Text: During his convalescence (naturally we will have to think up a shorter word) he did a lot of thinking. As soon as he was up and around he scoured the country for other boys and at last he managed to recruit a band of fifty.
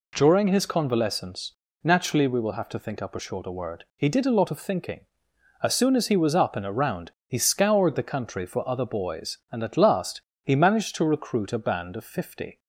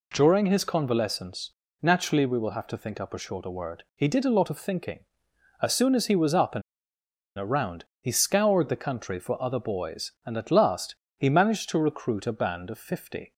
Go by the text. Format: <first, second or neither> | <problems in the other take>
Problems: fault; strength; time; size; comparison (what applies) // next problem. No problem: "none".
first | pauses between "and" and "around"; noticeable; at 6.6 s; 0.74 s long // pauses between "around" and "he"; slight; at 7.8 s; 0.16 s long; slight in the first // pauses between "last" and "he"; slight; at 10.9 s; 0.22 s long; slight in the first